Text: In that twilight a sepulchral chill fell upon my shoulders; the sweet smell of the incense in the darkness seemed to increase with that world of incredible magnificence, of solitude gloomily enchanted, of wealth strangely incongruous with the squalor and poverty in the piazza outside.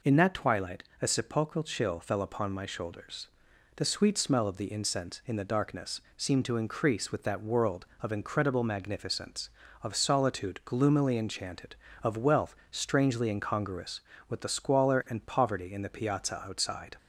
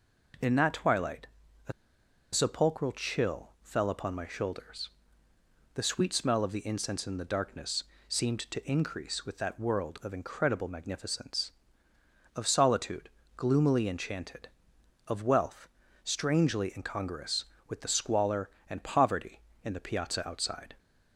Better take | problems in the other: first | pauses between "twilight" and "a"; at 1.2 s; 0.40 s long; slight in the first // pauses between "a" and "sepulchral"; noticeable; at 1.7 s; 0.61 s long // pauses between "darkness" and "seemed"; slight; at 7.8 s; 0.24 s long // pauses between "solitude" and "gloomily"; slight; at 13.0 s; 0.26 s long // pauses between "wealth" and "strangely"; at 15.6 s; 0.38 s long; slight in the first

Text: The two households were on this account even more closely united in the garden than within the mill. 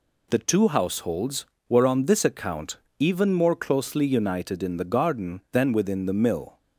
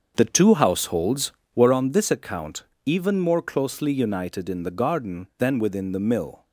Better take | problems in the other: first | starts louder than the rest; until 1.8 s; 7 dB // pauses between "account" and "even"; slight; at 2.6 s; 0.22 s long; slight in the first

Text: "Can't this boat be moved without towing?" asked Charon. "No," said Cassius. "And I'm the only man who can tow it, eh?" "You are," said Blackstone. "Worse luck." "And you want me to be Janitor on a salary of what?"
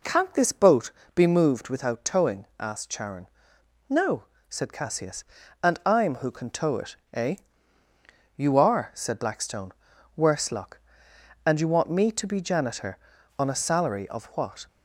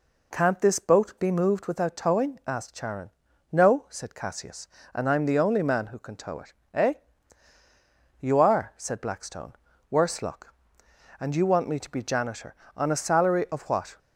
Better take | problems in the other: second | pauses between "boat" and "be"; slight; at 0.9 s; 0.24 s long // skips "the only man"; at 6.1 s

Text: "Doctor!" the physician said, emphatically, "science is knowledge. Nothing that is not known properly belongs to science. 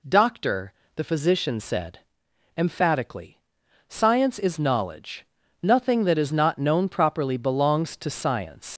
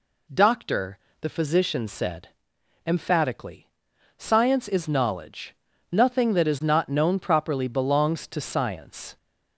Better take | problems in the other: second | leaves "science" unfinished; at 8.7 s; 100 ms

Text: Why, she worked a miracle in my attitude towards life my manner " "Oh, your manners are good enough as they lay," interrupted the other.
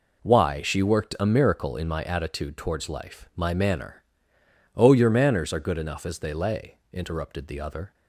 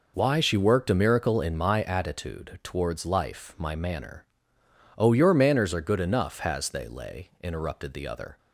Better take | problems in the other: first | says "has" for "as"; at 6.3 s

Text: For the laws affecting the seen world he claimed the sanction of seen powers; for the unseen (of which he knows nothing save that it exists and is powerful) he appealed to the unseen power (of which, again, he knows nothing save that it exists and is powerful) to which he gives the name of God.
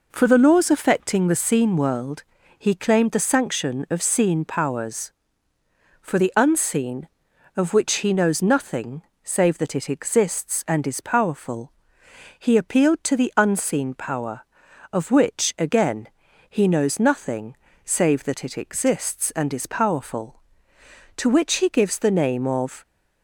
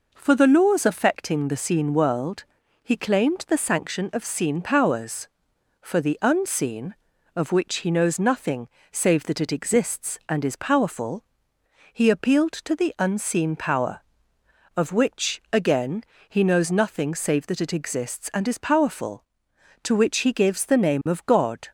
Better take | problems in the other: second | pauses between "world" and "he"; slight; at 2.2 s; 0.36 s long; also in the second // pauses between "nothing" and "save"; slight; at 9.0 s; 0.20 s long; slight in the second // pauses between "nothing" and "save"; slight; at 17.5 s; 0.30 s long // stops before "God"; at 22.8 s

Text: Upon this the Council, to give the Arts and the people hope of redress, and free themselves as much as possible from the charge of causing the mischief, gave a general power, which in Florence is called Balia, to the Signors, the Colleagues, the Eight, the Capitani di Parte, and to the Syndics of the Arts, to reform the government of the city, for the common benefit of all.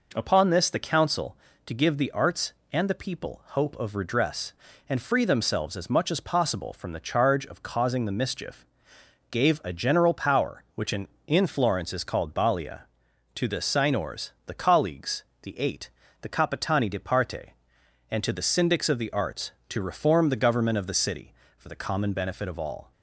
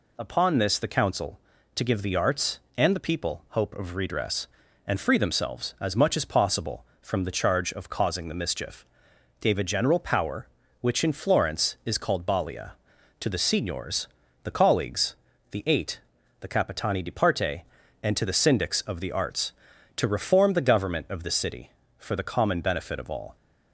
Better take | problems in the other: second | says "in" twice; at 11.2 s

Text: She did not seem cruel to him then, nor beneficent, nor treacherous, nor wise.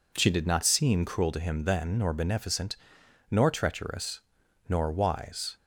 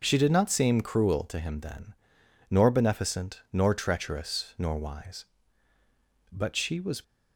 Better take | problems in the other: first | starts louder than the rest; noticeable; until 1.0 s; 6 dB // goes on to say "But she was"; noticeable; from 6.3 s on; 0.72 s long

